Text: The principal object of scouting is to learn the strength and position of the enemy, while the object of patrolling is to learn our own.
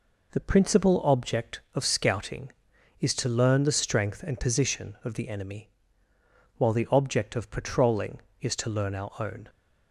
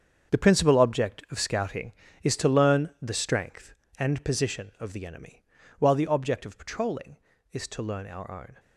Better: first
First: none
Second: gets quieter; strong; throughout; 13 dB

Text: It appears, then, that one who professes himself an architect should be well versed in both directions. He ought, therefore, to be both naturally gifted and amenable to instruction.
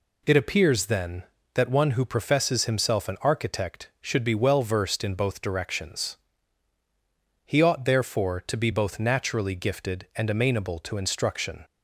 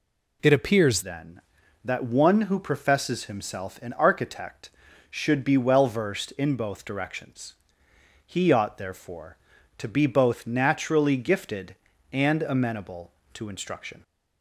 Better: first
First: none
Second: changes voice at "then"; from 1.0 s on; 13.0 s long

